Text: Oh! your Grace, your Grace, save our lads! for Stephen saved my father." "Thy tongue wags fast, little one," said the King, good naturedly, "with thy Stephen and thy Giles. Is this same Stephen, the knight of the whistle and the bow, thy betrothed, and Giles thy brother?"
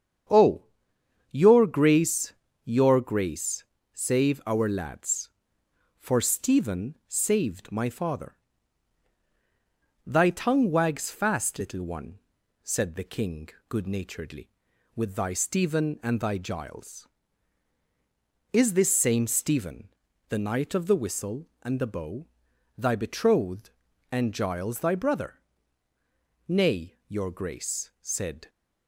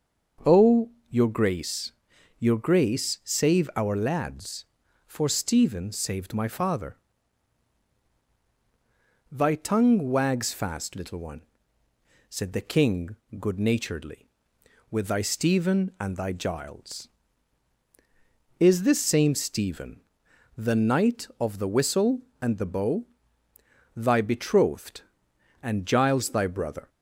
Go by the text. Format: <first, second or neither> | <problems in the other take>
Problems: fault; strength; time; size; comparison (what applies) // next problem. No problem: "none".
second | starts louder than the rest; strong; until 1.9 s; 8 dB; noticeable in the second // goes on to say "Nay your Grace said"; strong; from 26.4 s on; 2.0 s long